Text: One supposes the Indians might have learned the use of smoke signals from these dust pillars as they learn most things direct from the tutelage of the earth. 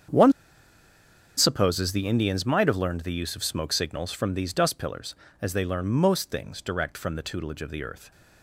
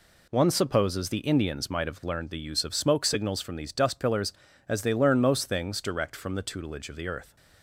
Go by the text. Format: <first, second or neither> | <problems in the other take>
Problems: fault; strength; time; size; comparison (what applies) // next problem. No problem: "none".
second | starts louder than the rest; strong; until 2.1 s; 7.5 dB // pauses between "One" and "supposes"; at 0.3 s; 1.0 s long